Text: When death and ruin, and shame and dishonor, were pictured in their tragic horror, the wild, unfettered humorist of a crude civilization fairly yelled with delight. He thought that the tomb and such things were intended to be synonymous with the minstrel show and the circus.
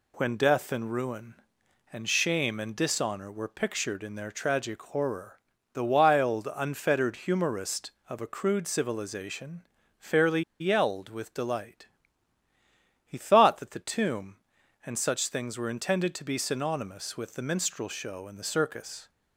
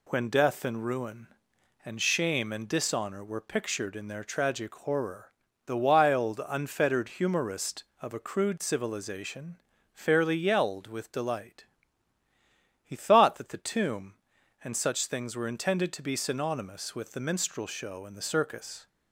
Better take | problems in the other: second | pauses between "civilization" and "fairly"; slight; at 9.6 s; 0.36 s long; slight in the second // pauses between "fairly" and "yelled"; slight; at 10.4 s; 0.19 s long

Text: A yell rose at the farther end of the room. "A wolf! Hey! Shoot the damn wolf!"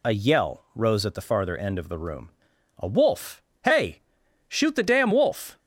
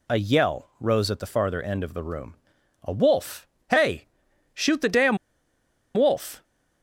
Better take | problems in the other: first | pauses between "damn" and "wolf"; noticeable; at 5.1 s; 0.77 s long

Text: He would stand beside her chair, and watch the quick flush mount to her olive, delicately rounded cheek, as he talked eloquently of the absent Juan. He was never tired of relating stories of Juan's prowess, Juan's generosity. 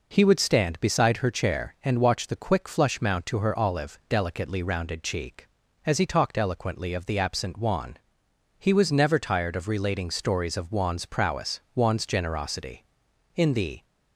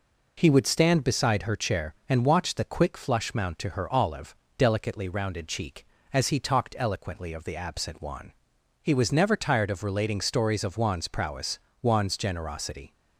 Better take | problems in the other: second | goes on to say "In the"; slight; from 13.3 s on; 0.48 s long

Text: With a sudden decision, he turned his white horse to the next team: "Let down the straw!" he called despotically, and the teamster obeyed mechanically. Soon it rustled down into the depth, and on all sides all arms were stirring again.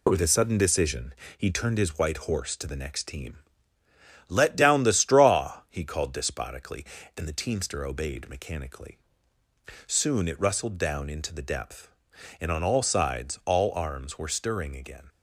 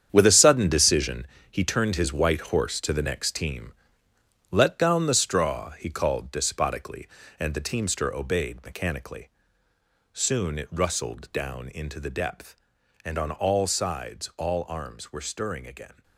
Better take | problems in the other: first | gets quieter; strong; throughout; 11 dB

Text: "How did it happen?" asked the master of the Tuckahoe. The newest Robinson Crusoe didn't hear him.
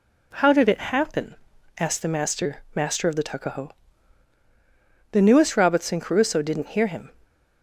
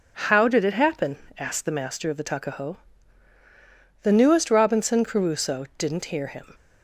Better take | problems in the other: second | says "master" twice; at 2.7 s

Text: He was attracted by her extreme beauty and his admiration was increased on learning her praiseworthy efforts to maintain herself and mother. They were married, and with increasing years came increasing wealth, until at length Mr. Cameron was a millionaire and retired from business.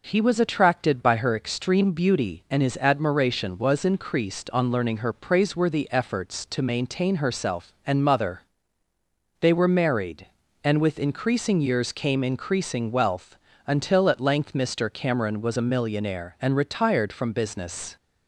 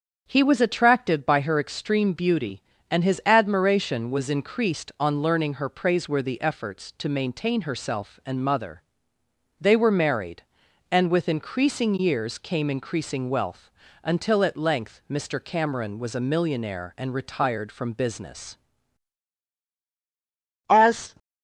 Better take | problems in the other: first | starts louder than the rest; strong; until 1.2 s; 7 dB // goes on to say "As"; slight; from 20.6 s on; 0.44 s long

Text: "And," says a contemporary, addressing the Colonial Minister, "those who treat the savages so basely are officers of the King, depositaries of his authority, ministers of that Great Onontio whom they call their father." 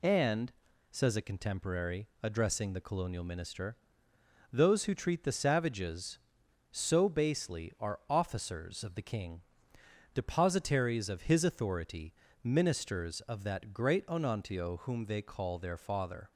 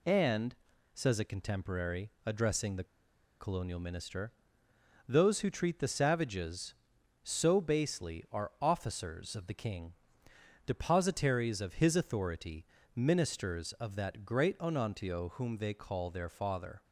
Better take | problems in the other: first | pauses between "the" and "Colonial"; noticeable; at 2.8 s; 0.55 s long

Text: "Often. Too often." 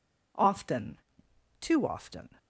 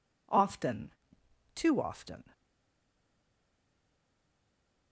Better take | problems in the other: first | stays silent after the last word; strong; from 2.3 s on; 2.6 s long

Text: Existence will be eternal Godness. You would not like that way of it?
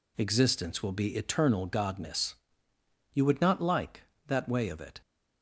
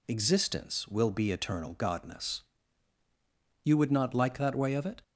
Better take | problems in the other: neither | none

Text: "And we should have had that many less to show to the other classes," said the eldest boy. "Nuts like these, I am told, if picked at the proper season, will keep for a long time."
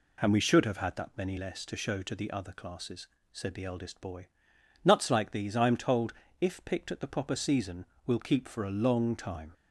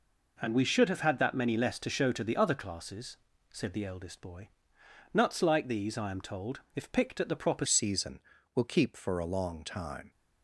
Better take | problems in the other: first | changes voice at "season"; from 7.6 s on; 2.5 s long

